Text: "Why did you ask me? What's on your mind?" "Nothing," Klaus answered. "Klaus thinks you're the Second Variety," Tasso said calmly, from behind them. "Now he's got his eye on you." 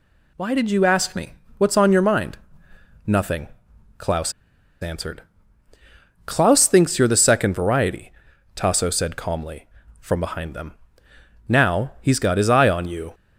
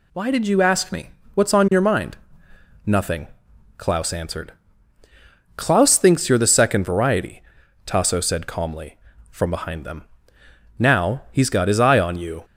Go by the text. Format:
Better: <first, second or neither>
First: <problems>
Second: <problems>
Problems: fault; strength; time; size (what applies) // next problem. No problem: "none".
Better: second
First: pauses between "Klaus" and "answered"; noticeable; at 4.3 s; 0.49 s long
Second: none